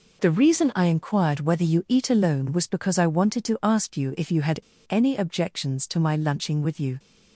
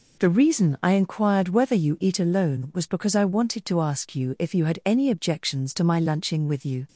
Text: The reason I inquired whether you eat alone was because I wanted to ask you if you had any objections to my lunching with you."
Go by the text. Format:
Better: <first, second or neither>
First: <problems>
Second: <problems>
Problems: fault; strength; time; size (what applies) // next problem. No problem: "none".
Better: second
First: pauses between "had" and "any"; slight; at 4.6 s; 0.29 s long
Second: none